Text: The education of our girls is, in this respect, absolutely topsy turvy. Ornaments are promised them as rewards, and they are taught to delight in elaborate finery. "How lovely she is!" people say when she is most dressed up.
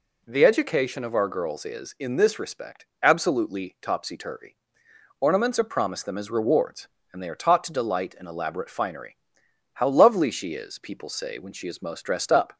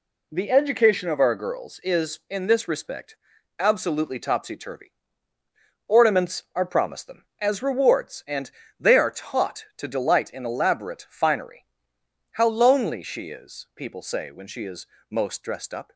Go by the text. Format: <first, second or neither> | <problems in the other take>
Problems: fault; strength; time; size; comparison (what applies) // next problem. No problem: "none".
first | pauses between "and" and "they"; slight; at 8.5 s; 0.28 s long // says "lonely" for "lovely"; at 12.4 s // pauses between "is" and "most"; slight; at 14.8 s; 0.24 s long